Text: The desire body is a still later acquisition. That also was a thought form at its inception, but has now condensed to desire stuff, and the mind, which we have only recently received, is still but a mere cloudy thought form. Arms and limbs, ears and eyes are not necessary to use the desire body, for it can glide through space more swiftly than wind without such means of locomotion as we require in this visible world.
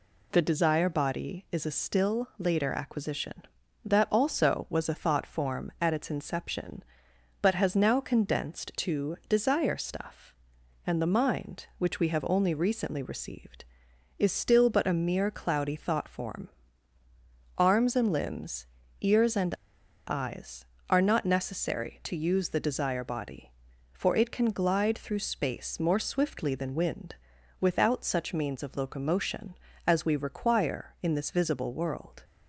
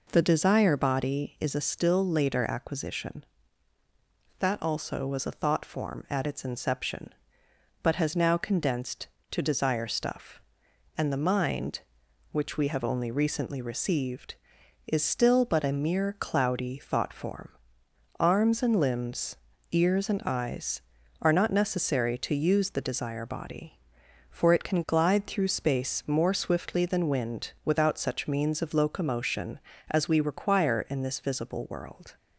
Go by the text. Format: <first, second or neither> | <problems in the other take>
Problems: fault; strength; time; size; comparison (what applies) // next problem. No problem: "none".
second | pauses between "and" and "eyes"; noticeable; at 19.5 s; 0.54 s long // pauses between "wind" and "without"; noticeable; at 27.1 s; 0.46 s long